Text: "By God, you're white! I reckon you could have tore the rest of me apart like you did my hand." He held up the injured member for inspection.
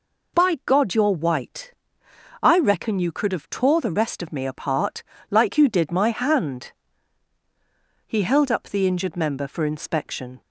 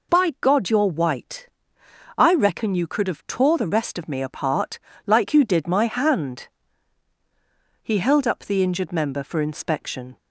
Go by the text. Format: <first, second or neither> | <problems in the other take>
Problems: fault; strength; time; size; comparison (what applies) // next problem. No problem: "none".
neither | pauses between "apart" and "like"; slight; the same in both